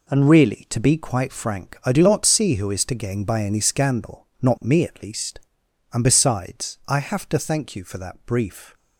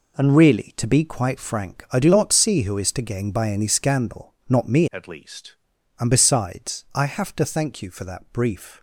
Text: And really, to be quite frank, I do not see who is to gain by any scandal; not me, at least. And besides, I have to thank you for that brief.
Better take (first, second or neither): first